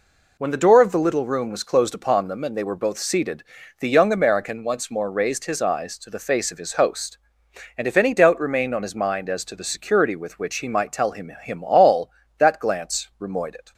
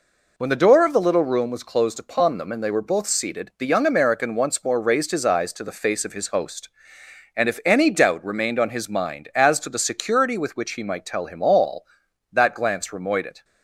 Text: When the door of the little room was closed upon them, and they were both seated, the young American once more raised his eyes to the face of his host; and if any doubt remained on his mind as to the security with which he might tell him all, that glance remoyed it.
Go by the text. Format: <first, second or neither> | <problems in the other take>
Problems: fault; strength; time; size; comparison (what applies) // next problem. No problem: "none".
second | says "him" twice; at 11.4 s